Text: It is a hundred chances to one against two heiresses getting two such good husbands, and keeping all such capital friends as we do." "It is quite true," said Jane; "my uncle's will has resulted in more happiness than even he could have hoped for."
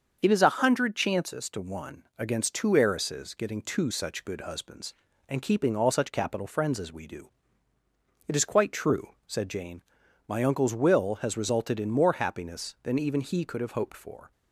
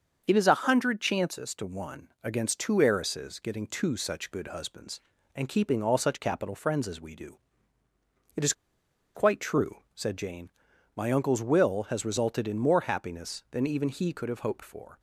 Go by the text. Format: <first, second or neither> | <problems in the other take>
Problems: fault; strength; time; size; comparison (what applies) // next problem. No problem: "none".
first | starts louder than the rest; until 1.2 s; 6.5 dB; also in the first // pauses between "one" and "against"; slight; at 2.0 s; 0.16 s long; slight in the first // pauses between "is" and "quite"; noticeable; at 8.5 s; 0.61 s long